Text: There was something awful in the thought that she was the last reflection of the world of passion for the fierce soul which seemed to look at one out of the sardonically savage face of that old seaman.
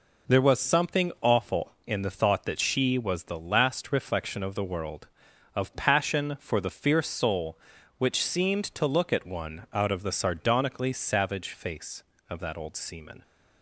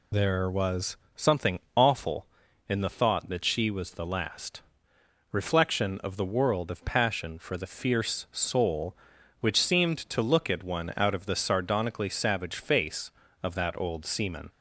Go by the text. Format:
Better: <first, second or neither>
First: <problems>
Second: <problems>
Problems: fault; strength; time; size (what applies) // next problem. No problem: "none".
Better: first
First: none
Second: loses the start of "There"; at 0.1 s; 50 ms // pauses between "was" and "something"; slight; at 0.9 s; 0.20 s long // pauses between "something" and "awful"; slight; at 1.5 s; 0.18 s long // pauses between "last" and "reflection"; noticeable; at 4.6 s; 0.70 s long